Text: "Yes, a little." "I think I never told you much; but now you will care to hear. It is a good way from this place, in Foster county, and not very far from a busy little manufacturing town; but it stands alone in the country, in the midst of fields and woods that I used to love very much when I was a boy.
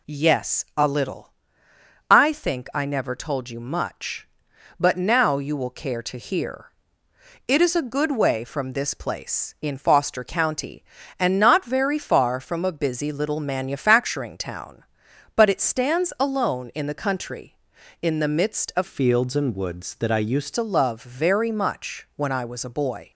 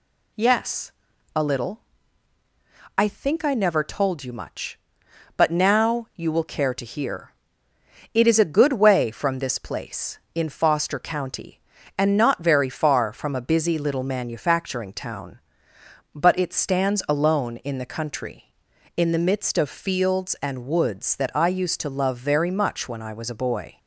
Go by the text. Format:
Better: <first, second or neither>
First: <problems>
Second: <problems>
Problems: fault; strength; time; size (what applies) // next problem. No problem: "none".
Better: second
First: changes voice from "fields" to "used"; from 18.8 to 20.5 s; 1.7 s long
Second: none